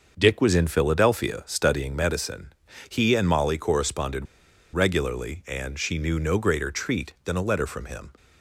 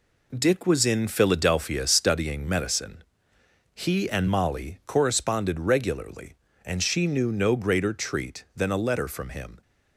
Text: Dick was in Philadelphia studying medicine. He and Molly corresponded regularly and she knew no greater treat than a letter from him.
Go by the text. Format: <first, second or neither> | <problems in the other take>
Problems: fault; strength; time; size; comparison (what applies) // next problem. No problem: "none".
second | starts louder than the rest; until 1.1 s; 6 dB // pauses between "corresponded" and "regularly"; noticeable; at 4.2 s; 0.49 s long